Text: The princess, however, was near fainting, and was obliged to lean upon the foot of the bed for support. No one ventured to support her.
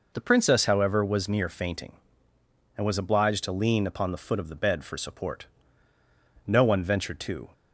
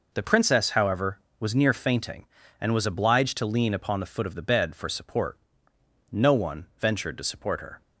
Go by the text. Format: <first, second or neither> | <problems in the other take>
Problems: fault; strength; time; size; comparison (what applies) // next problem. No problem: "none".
second | stops before "support her"; at 7.5 s